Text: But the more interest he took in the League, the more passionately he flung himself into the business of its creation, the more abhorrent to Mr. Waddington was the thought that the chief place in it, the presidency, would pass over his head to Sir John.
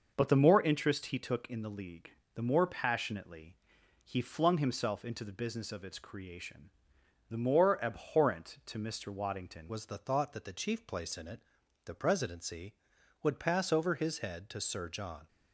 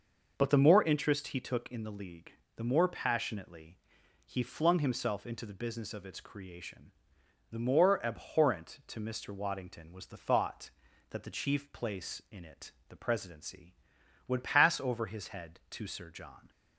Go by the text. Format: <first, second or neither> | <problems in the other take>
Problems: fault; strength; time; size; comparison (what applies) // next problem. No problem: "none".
second | pauses between "passionately" and "he"; noticeable; at 3.5 s; 0.48 s long; noticeable in the second // changes voice at "was"; from 9.6 s on; 5.6 s long